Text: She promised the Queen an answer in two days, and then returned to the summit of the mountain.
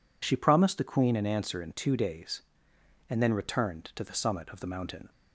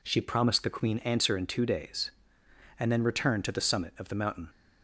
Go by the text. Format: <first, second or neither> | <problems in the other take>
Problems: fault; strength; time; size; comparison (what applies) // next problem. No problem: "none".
first | skips "an"; at 0.9 s